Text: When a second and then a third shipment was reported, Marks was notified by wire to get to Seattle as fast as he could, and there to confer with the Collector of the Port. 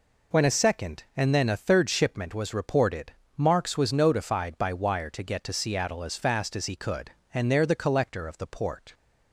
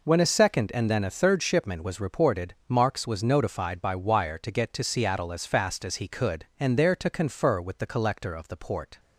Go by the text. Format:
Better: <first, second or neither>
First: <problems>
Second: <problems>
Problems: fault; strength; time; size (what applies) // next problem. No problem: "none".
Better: second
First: skips "to confer with"; at 7.6 s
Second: none